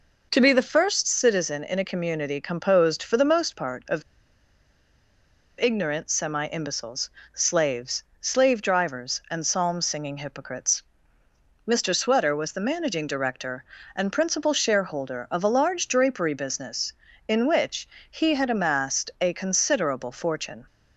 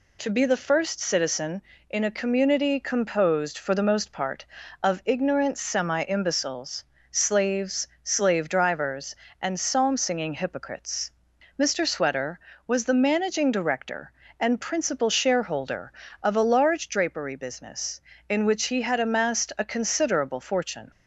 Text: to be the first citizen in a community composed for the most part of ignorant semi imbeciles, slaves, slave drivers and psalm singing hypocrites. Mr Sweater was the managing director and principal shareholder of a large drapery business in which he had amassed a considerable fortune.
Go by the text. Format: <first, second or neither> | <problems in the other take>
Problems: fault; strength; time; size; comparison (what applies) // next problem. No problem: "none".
second | pauses between "of" and "ignorant"; strong; at 4.0 s; 1.5 s long // pauses between "which" and "he"; slight; at 17.8 s; 0.24 s long